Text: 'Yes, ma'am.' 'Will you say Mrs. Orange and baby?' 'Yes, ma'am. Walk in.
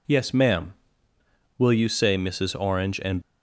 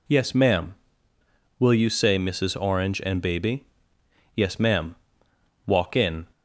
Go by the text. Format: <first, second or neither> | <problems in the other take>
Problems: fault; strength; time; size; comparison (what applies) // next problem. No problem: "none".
second | stops before "baby Yes ma'am Walk in"; at 3.2 s